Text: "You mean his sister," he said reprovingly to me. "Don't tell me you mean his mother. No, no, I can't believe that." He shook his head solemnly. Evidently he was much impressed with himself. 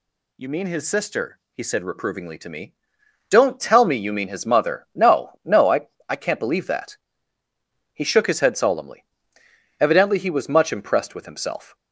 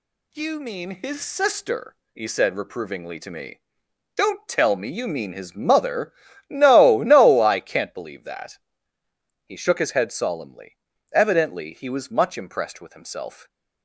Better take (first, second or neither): second